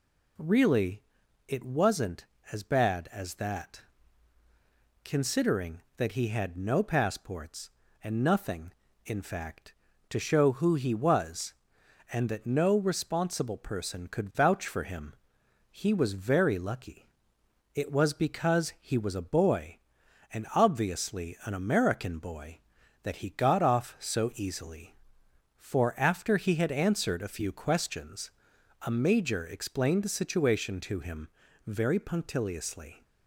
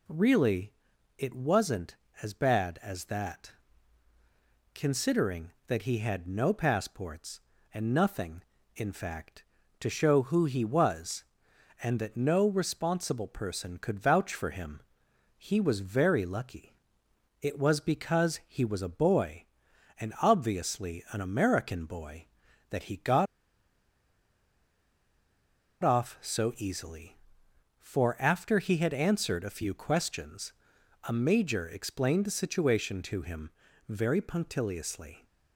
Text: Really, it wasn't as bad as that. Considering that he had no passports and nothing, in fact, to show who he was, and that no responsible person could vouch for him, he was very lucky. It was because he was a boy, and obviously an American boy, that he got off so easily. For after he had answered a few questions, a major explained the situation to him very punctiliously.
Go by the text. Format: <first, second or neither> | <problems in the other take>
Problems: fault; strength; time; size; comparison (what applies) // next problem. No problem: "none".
first | pauses between "got" and "off"; strong; at 23.2 s; 2.5 s long // pauses between "him" and "very"; at 33.4 s; 0.40 s long; also in the first